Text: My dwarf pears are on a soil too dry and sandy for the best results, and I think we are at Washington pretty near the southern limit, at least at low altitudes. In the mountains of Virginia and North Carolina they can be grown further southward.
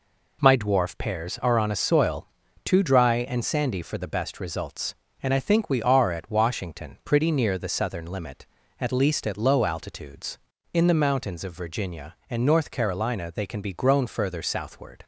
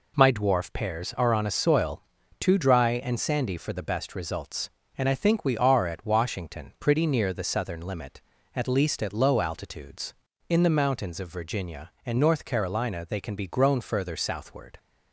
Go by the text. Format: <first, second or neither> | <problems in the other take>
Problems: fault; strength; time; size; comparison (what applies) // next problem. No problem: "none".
neither | pauses between "soil" and "too"; the same in both